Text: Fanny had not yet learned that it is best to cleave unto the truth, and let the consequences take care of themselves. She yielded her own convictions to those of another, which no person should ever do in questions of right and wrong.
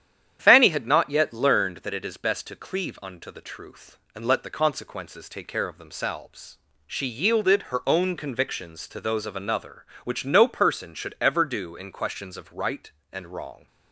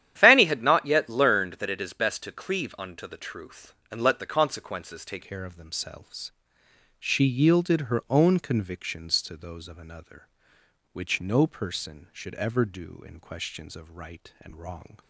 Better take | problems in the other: first | starts louder than the rest; strong; until 1.1 s; 10.5 dB; strong in the first // changes voice at "care"; from 5.2 s on; 9.7 s long

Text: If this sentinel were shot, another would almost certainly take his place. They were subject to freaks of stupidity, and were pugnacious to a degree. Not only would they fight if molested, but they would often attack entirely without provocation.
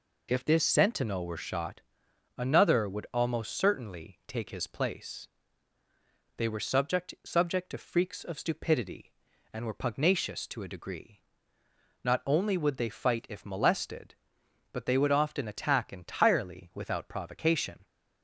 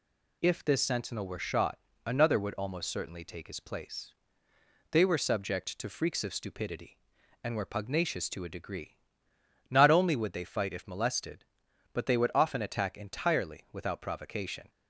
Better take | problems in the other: second | says "subject" twice; at 7.2 s

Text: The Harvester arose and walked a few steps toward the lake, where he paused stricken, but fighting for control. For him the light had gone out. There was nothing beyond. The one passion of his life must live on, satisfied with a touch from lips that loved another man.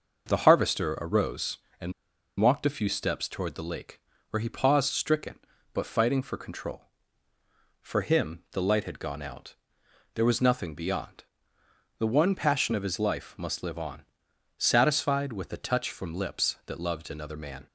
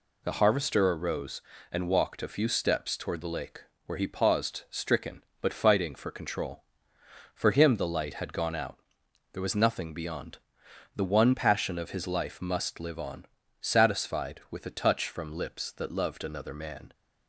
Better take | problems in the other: second | pauses between "and" and "walked"; noticeable; at 1.9 s; 0.48 s long

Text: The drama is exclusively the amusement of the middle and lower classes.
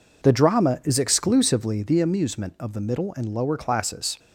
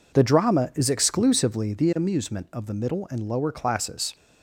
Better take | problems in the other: neither | none

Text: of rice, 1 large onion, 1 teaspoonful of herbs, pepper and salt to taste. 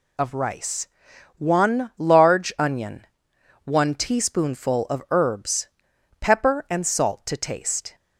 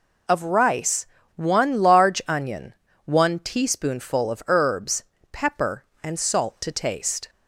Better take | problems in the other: neither | none

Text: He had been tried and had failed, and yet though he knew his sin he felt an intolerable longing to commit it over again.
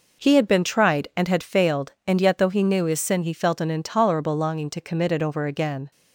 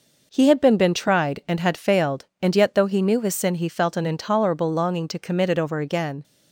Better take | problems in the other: first | says "been" twice; at 0.7 s

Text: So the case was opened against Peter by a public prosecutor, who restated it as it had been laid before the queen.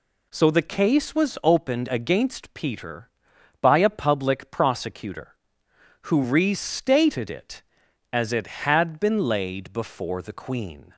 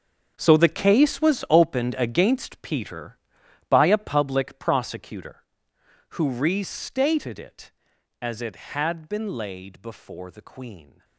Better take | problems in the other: first | gets quieter; strong; throughout; 14.5 dB

